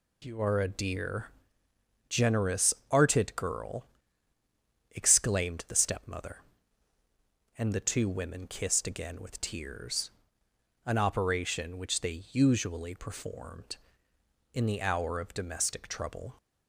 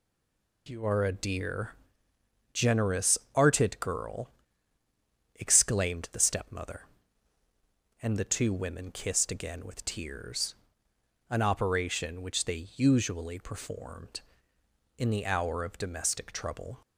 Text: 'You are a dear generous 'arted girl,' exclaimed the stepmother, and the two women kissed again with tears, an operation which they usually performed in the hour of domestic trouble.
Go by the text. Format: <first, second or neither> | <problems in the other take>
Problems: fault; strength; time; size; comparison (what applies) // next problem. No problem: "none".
first | stays silent before the first word; slight; until 0.6 s; 0.6 s long // pauses between "dear" and "generous"; noticeable; at 1.7 s; 0.78 s long; noticeable in the first // pauses between "generous" and "arted"; slight; at 3.1 s; 0.18 s long; slight in the first